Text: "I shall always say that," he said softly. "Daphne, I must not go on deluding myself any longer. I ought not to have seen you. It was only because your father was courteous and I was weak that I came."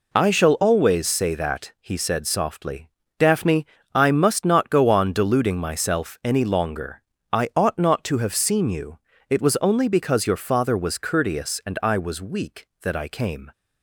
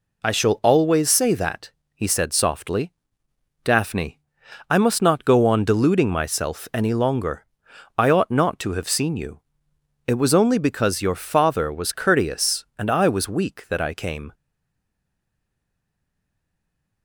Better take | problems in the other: first | stays silent after the last word; strong; from 14.3 s on; 2.7 s long

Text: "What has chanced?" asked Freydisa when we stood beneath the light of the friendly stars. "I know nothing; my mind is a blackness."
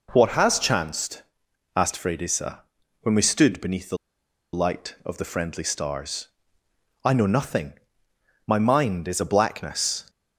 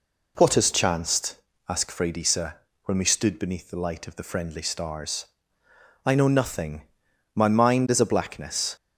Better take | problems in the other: second | pauses between "Freydisa" and "when"; at 2.6 s; 0.38 s long; slight in the second // pauses between "the" and "light"; noticeable; at 3.9 s; 0.56 s long

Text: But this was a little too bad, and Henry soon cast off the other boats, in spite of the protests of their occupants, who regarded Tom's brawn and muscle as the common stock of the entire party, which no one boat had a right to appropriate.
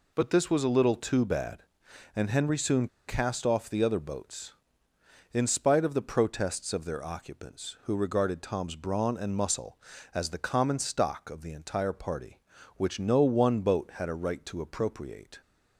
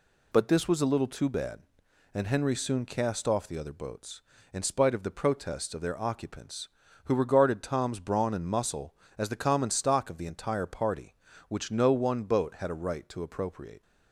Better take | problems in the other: second | pauses between "soon" and "cast"; slight; at 2.8 s; 0.20 s long

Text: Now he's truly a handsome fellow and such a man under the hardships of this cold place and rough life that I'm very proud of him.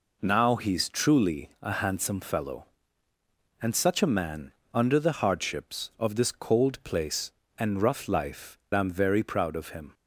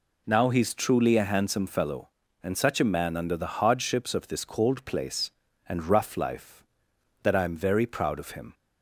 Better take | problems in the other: second | pauses between "man" and "under"; slight; at 4.5 s; 0.22 s long // skips "that"; at 8.6 s

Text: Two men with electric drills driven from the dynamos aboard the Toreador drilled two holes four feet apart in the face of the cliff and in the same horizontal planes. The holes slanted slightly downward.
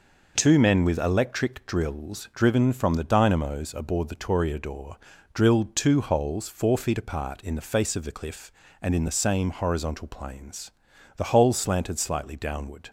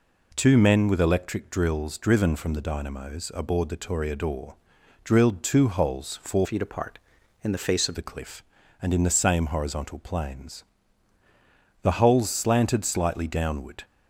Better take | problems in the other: first | pauses between "Toreador" and "drilled"; noticeable; at 4.5 s; 0.48 s long; slight in the first // changes voice from "feet" to "of"; from 6.4 to 7.9 s; 1.5 s long

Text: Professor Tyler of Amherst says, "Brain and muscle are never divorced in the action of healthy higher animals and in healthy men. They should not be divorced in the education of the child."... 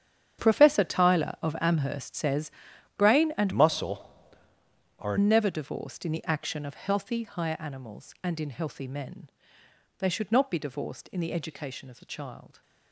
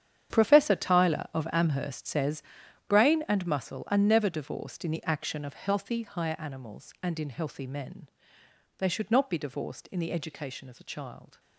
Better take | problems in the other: second | starts louder than the rest; strong; until 1.4 s; 9 dB; strong in the second // changes voice from "muscle" to "are"; from 3.5 to 5.1 s; 1.6 s long

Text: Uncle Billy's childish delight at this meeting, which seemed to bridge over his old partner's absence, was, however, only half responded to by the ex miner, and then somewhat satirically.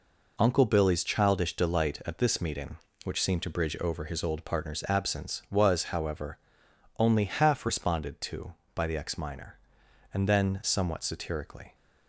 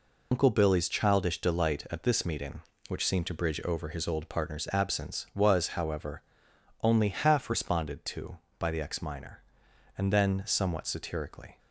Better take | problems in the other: first | loses the start of "Uncle"; at 0.3 s; 80 ms

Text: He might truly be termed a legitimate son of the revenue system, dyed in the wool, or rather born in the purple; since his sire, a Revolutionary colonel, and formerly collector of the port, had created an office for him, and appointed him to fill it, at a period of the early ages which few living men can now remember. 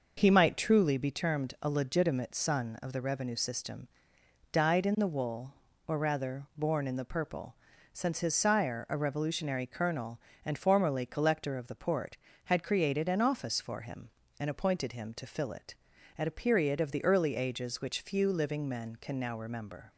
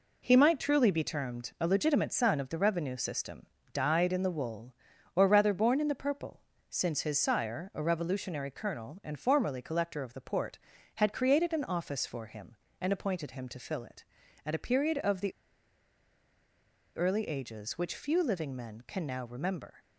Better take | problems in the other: first | pauses between "the" and "early"; strong; at 15.3 s; 1.6 s long

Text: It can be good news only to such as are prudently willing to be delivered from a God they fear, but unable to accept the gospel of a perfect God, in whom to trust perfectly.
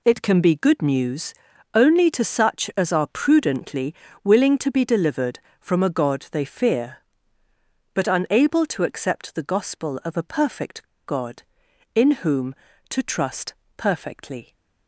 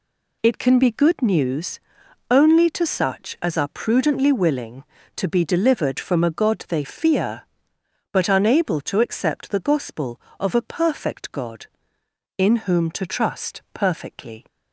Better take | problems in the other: second | pauses between "news" and "only"; at 1.3 s; 0.42 s long; noticeable in the second // pauses between "prudently" and "willing"; slight; at 3.9 s; 0.30 s long // pauses between "perfect" and "God"; slight; at 10.8 s; 0.21 s long // pauses between "trust" and "perfectly"; slight; at 13.5 s; 0.24 s long

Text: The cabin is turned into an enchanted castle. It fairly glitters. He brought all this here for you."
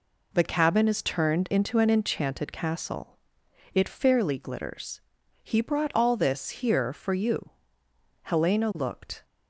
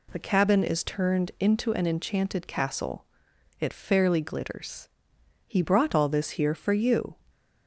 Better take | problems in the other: second | goes on to say "Helena looked"; noticeable; from 8.2 s on; 1.0 s long

